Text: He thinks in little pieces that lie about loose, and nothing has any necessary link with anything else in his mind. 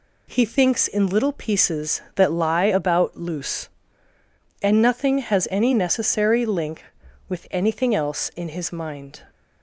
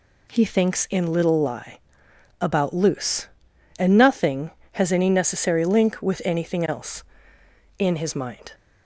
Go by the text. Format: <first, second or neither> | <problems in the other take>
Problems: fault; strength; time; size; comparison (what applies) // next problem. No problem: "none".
first | skips "pieces that"; at 1.4 s // pauses between "lie" and "about"; noticeable; at 1.7 s; 0.60 s long